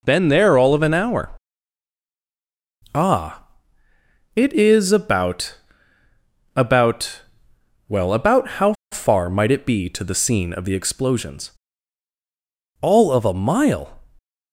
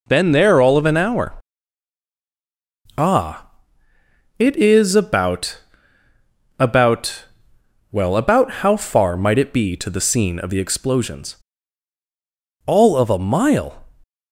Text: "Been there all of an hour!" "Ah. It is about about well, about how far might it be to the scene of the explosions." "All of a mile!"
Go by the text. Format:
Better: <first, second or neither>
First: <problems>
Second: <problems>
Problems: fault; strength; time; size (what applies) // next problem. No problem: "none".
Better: second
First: pauses between "about" and "about"; noticeable; at 5.5 s; 0.98 s long // pauses between "about" and "well"; noticeable; at 7.2 s; 0.66 s long // pauses between "how" and "far"; slight; at 8.7 s; 0.18 s long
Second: pauses between "about" and "about"; noticeable; at 5.6 s; 0.98 s long // pauses between "about" and "well"; noticeable; at 7.2 s; 0.66 s long